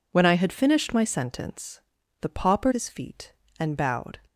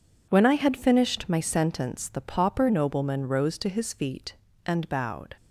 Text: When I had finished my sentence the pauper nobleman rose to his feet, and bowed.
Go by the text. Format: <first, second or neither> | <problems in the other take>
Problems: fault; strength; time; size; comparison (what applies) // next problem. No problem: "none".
second | pauses between "sentence" and "the"; at 1.7 s; 0.42 s long // skips "nobleman rose to"; at 2.7 s